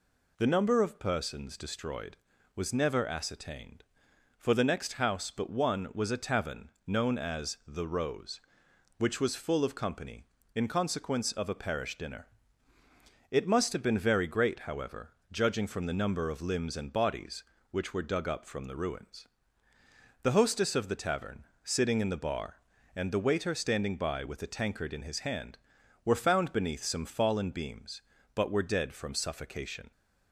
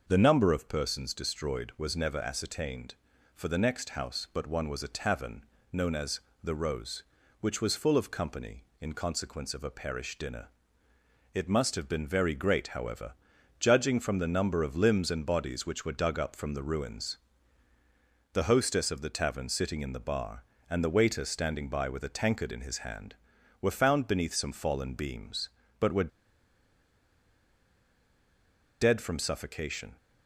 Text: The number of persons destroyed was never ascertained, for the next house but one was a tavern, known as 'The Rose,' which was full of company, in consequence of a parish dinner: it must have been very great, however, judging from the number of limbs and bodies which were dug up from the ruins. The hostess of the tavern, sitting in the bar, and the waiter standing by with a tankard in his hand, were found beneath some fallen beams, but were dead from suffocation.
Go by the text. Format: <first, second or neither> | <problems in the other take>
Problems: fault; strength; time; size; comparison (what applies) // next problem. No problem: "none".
first | starts louder than the rest; noticeable; until 1.0 s; 6 dB // pauses between "as" and "The"; slight; at 6.2 s; 0.22 s long // pauses between "were" and "dead"; strong; at 26.1 s; 2.7 s long